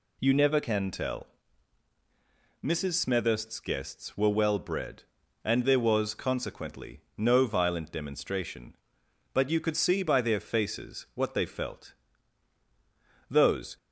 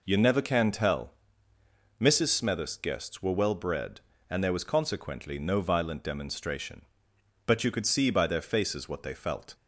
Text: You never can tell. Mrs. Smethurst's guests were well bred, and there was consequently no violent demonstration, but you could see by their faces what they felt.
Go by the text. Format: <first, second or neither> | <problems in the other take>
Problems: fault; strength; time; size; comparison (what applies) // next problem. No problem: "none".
second | pauses between "consequently" and "no"; slight; at 6.9 s; 0.18 s long // goes on to say "Those"; slight; from 13.3 s on; 0.46 s long